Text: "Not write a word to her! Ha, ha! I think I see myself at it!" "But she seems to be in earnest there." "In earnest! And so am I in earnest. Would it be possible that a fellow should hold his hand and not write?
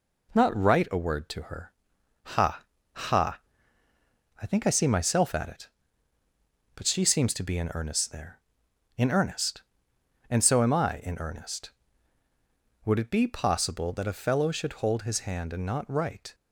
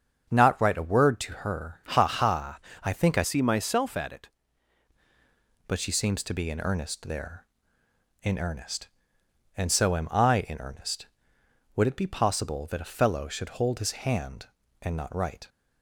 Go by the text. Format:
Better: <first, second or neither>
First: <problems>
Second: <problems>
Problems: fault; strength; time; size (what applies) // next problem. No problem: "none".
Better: first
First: none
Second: starts louder than the rest; strong; until 1.3 s; 7 dB // changes voice from "see" to "it"; from 3.2 to 4.2 s; 1.0 s long